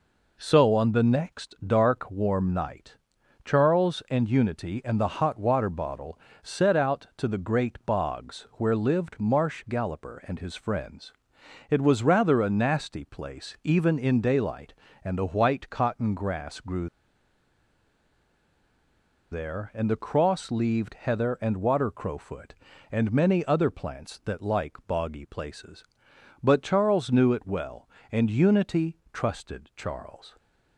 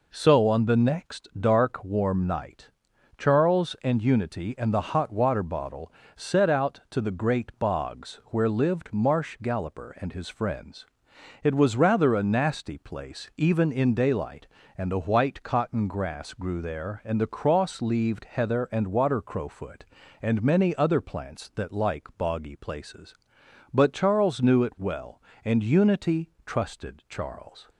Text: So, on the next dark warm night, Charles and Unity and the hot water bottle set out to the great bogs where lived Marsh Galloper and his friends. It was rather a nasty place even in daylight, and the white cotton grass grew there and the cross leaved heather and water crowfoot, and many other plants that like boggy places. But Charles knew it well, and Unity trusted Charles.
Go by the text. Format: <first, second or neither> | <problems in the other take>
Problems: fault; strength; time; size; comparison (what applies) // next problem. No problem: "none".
second | pauses between "bottle" and "set"; slight; at 6.1 s; 0.24 s long; slight in the second // pauses between "grew" and "there"; strong; at 16.8 s; 2.4 s long // pauses between "Unity" and "trusted"; slight; at 28.9 s; 0.16 s long; slight in the second